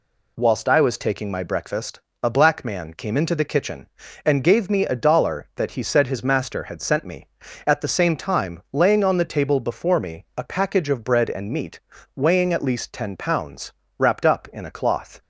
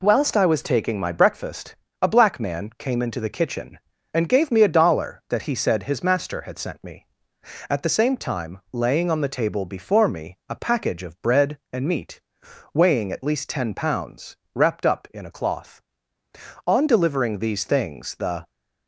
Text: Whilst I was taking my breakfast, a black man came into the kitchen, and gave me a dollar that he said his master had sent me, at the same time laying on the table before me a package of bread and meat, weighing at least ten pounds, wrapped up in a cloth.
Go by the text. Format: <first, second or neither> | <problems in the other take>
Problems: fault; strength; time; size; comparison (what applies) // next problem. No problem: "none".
first | goes on to say "On delivering these things the"; strong; from 16.6 s on; 1.8 s long